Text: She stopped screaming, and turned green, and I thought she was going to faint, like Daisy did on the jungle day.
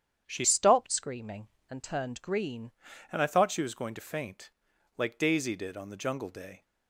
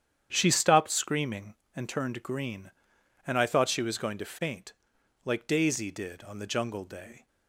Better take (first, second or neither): second